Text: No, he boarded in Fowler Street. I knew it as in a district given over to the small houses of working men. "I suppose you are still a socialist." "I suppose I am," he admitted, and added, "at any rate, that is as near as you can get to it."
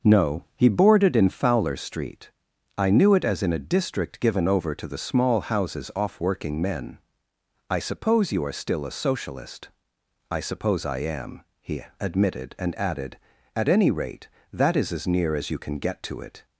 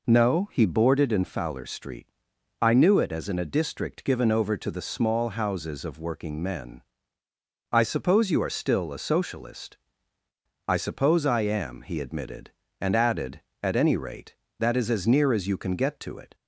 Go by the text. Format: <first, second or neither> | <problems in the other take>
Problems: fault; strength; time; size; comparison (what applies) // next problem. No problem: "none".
second | says "off" for "of"; at 5.9 s // pauses between "he" and "admitted"; slight; at 11.8 s; 0.16 s long